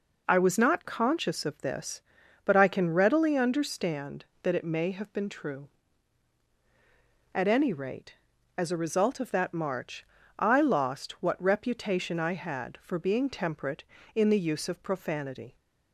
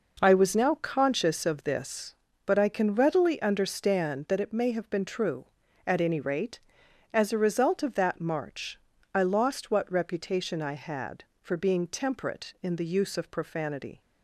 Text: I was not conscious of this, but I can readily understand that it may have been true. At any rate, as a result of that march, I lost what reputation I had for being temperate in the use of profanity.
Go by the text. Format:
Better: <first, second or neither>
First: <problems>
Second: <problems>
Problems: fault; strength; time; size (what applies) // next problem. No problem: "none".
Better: first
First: none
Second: says "now" for "not"; at 0.5 s